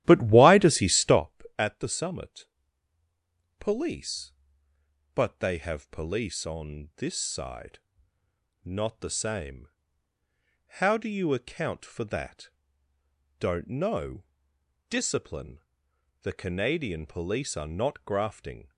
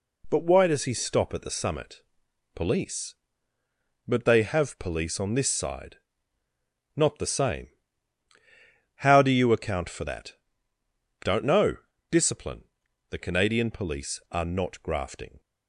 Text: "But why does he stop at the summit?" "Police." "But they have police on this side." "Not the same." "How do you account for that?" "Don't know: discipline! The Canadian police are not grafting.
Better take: second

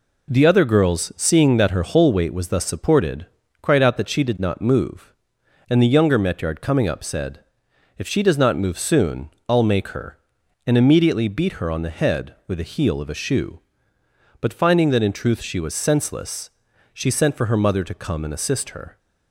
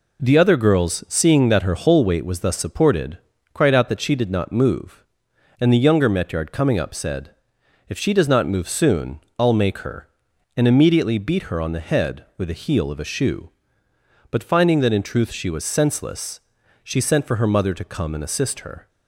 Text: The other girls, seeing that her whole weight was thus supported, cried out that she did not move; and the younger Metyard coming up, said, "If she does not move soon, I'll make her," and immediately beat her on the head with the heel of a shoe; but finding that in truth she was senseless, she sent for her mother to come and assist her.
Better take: neither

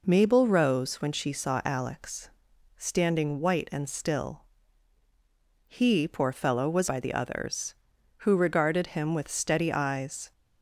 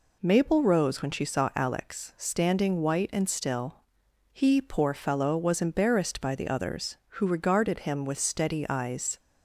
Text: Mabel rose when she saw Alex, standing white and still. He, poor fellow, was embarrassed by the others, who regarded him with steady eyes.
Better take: second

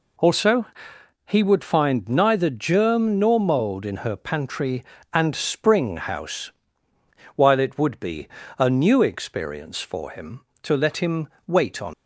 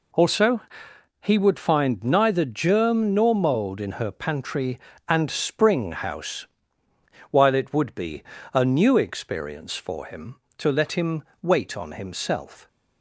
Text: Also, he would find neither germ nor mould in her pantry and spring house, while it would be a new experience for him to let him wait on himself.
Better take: second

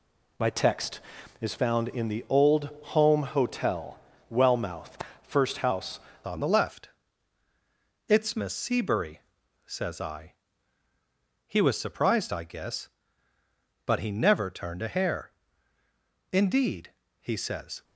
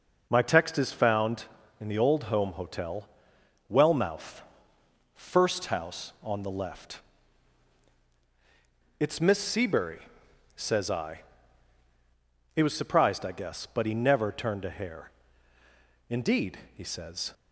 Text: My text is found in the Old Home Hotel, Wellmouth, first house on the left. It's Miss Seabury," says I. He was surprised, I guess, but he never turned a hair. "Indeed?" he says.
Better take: second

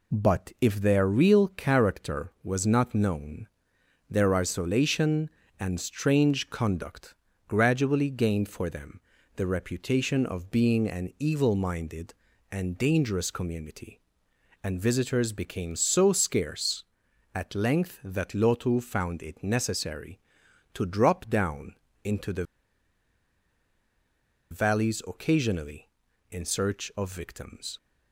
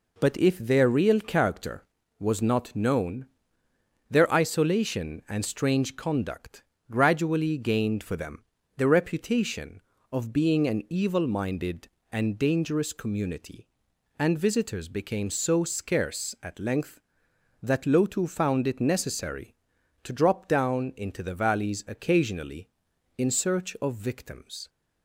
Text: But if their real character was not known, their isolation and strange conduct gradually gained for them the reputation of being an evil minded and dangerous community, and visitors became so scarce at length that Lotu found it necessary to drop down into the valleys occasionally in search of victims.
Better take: second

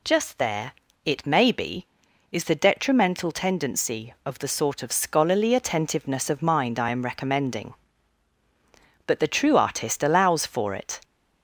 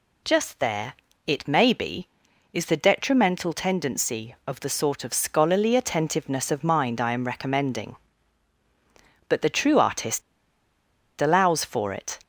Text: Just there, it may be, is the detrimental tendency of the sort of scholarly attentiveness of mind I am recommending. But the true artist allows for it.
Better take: first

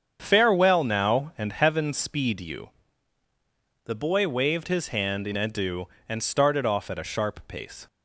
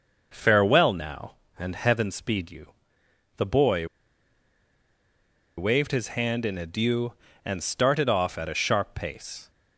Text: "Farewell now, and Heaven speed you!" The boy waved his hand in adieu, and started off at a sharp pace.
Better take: first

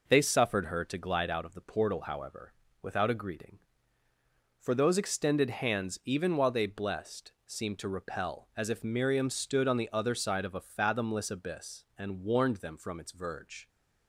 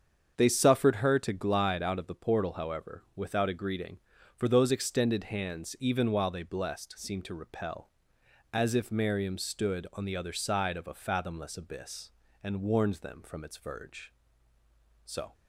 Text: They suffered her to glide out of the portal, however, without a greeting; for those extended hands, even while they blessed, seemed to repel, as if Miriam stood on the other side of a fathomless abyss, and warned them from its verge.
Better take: first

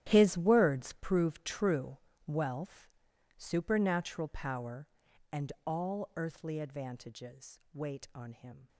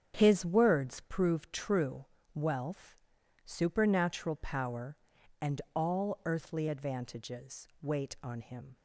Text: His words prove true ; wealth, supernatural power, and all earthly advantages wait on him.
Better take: second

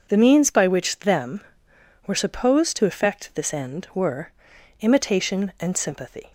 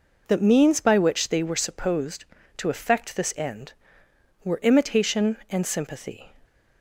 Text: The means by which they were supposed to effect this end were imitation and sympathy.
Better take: second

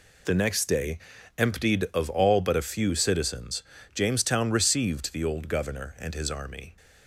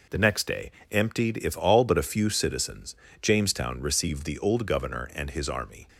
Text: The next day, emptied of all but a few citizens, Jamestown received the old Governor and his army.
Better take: first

